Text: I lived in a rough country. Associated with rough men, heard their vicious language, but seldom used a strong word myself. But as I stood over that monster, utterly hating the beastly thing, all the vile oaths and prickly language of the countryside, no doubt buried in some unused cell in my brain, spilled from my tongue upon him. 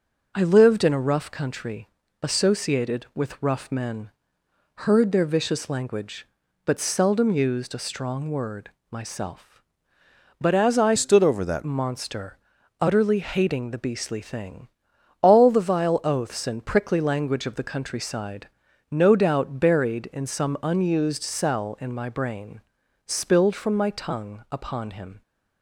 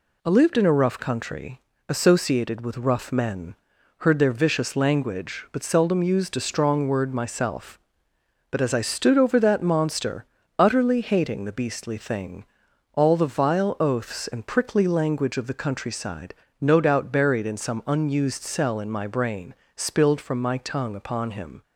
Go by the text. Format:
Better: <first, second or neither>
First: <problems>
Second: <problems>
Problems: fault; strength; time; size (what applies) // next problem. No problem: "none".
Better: second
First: pauses between "word" and "myself"; slight; at 8.7 s; 0.20 s long // changes voice from "stood" to "that"; from 10.9 to 11.6 s; 0.7 s long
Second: none